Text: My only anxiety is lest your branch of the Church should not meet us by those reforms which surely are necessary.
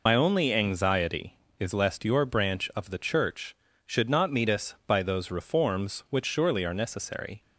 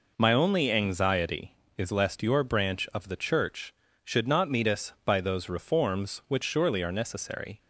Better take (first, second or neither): second